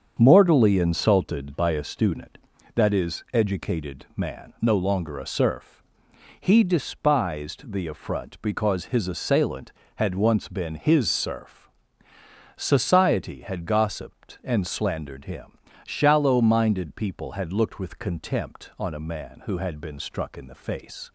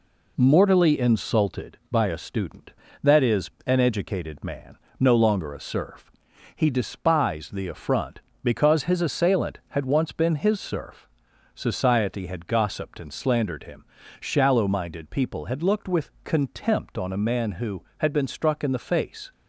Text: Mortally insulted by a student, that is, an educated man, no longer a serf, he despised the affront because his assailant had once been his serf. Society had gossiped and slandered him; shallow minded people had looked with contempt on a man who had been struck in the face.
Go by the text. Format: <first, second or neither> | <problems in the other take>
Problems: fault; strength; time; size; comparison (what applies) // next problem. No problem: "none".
second | starts louder than the rest; strong; until 1.2 s; 7.5 dB // skips "an"; at 3.2 s